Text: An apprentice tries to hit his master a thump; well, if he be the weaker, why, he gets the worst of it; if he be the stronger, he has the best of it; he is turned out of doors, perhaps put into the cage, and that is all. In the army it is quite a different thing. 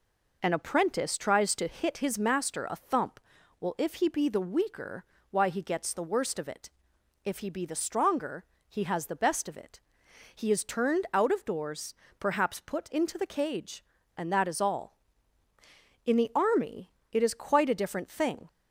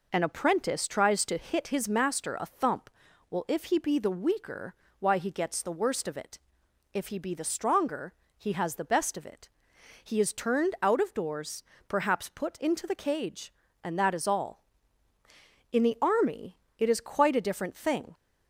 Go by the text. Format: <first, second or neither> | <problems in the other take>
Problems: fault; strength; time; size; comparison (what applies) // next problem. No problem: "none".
neither | pauses between "army" and "it"; slight; the same in both